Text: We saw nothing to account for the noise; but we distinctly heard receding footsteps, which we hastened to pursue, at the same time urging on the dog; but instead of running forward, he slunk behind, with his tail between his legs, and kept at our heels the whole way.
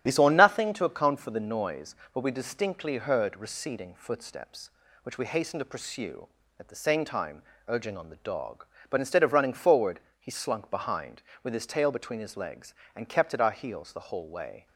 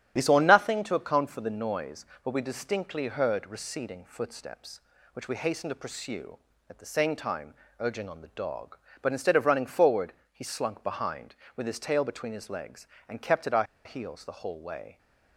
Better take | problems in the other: first | starts louder than the rest; strong; until 1.1 s; 10 dB; strong in the first // pauses between "time" and "urging"; slight; at 7.5 s; 0.28 s long; slight in the first // pauses between "our" and "heels"; slight; at 13.6 s; 0.20 s long

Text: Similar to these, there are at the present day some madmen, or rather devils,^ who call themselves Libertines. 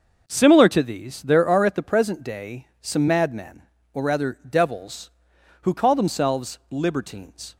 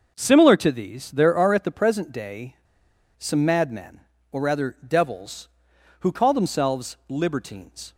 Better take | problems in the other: first | starts louder than the rest; noticeable; until 1.2 s; 6 dB; noticeable in the first // pauses between "day" and "some"; noticeable; at 2.5 s; 0.62 s long

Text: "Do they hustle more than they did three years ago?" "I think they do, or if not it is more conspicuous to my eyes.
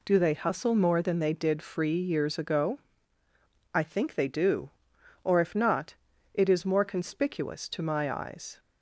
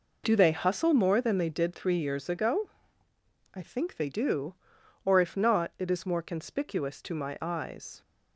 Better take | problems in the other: second | says "free" for "three"; at 1.6 s // pauses between "not" and "it"; at 5.9 s; 0.40 s long

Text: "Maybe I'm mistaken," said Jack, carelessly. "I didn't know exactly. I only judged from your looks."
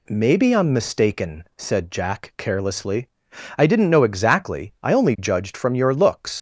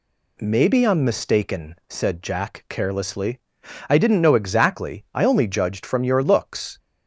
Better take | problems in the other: second | leaves "looks" unfinished; at 6.3 s; 100 ms

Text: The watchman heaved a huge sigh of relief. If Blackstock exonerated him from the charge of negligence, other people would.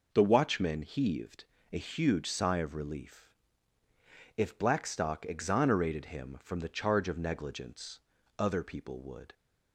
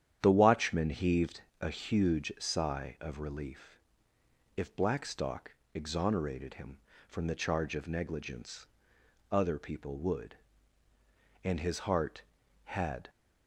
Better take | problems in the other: first | starts louder than the rest; strong; until 1.2 s; 9.5 dB // pauses between "heaved" and "a"; slight; at 1.4 s; 0.22 s long; slight in the first // pauses between "Blackstock" and "exonerated"; slight; at 5.5 s; 0.18 s long // goes on to say "And his heart had"; from 11.4 s on; 1.6 s long

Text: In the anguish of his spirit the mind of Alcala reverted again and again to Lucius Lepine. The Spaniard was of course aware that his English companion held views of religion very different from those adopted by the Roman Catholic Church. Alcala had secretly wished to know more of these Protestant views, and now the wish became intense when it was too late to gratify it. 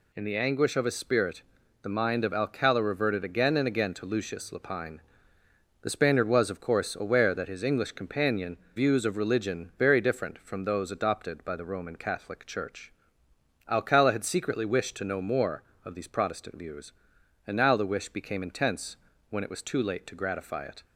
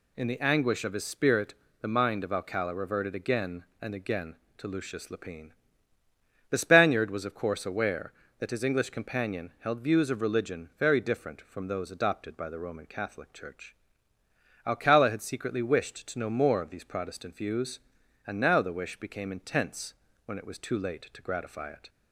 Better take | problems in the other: second | pauses between "spirit" and "the"; at 1.4 s; 0.40 s long; slight in the second // skips "held"; at 8.6 s // pauses between "intense" and "when"; slight; at 18.9 s; 0.32 s long; slight in the second

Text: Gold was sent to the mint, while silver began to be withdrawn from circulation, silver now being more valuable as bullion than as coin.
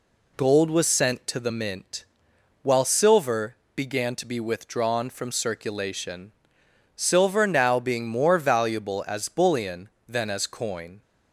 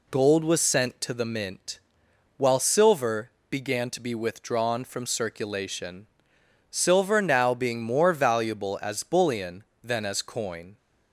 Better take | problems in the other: neither | pauses between "silver" and "began"; slight; the same in both

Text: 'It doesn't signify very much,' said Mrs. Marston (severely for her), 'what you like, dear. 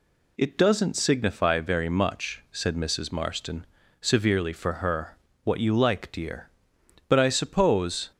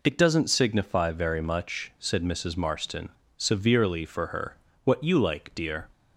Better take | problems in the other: second | goes on to say "But I suppose"; noticeable; from 7.0 s on; 1.0 s long

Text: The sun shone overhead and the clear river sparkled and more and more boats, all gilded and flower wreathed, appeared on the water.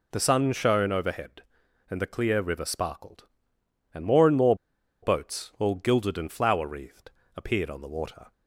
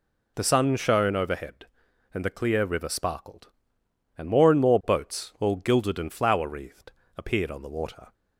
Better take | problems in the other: second | pauses between "more" and "boats"; noticeable; at 4.5 s; 0.47 s long

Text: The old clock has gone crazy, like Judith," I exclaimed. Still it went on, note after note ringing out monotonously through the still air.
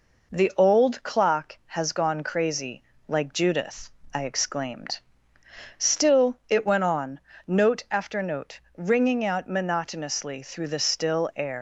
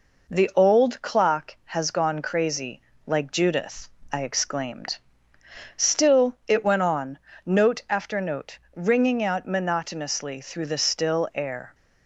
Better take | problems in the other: second | pauses between "note" and "ringing"; slight; at 8.5 s; 0.16 s long; slight in the second // leaves "air" unfinished; at 11.5 s; 140 ms

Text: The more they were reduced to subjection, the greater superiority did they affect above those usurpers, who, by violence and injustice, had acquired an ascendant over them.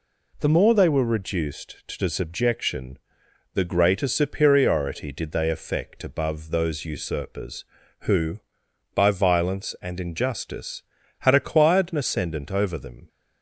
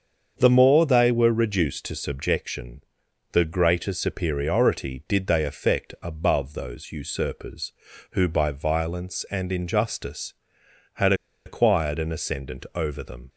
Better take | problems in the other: first | starts louder than the rest; until 1.3 s; 7 dB // pauses between "had" and "acquired"; slight; at 11.1 s; 0.32 s long

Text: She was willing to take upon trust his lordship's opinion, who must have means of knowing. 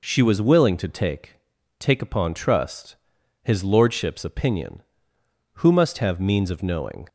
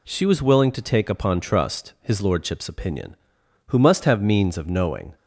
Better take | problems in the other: second | says "take" twice; at 1.7 s // pauses between "trust" and "his"; noticeable; at 2.9 s; 0.46 s long

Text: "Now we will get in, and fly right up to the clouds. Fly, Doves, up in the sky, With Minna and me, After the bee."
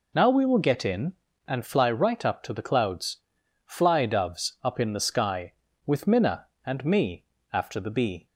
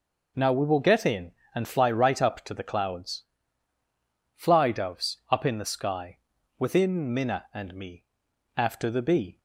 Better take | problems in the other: first | says "Within" for "With"; at 6.5 s

